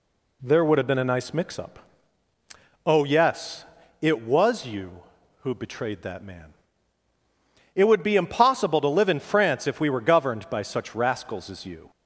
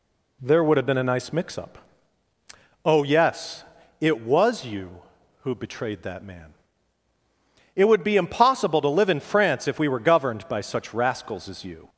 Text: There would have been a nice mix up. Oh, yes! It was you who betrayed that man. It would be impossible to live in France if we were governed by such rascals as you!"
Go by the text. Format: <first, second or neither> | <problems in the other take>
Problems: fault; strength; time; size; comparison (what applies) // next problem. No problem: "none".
neither | none